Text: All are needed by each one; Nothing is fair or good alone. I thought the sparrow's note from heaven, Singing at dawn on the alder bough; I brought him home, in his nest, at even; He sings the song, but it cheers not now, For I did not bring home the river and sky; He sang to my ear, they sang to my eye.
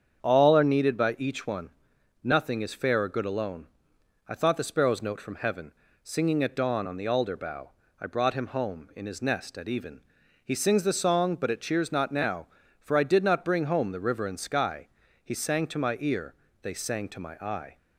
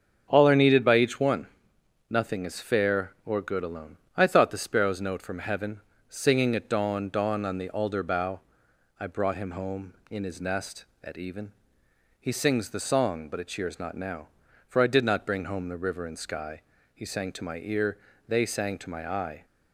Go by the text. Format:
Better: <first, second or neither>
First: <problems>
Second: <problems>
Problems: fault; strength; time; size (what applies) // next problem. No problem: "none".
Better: first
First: starts louder than the rest; strong; until 1.2 s; 7.5 dB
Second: starts louder than the rest; strong; until 1.3 s; 7 dB // says "dawn" twice; at 7.0 s